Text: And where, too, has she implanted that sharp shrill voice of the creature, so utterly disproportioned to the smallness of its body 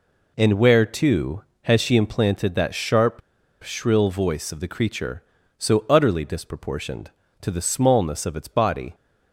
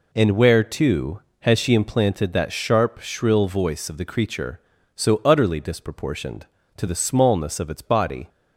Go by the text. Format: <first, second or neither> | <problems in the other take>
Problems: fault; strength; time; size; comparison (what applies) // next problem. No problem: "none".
second | pauses between "sharp" and "shrill"; at 3.2 s; 0.42 s long